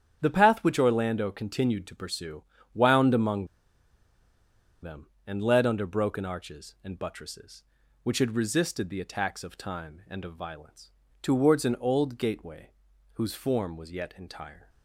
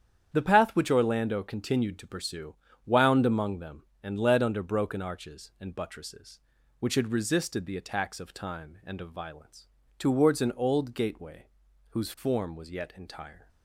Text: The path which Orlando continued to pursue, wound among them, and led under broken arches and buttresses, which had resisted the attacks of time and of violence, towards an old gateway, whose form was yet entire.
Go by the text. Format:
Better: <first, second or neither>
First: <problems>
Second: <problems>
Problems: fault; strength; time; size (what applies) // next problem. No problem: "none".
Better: second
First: starts louder than the rest; strong; until 1.2 s; 9 dB // pauses between "among" and "them"; strong; at 3.4 s; 1.3 s long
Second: starts louder than the rest; strong; until 1.3 s; 9 dB